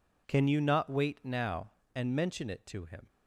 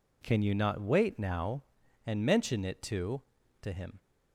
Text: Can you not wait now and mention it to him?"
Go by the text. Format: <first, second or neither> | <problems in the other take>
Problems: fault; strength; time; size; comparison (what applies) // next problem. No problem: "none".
first | says "to" twice; at 3.6 s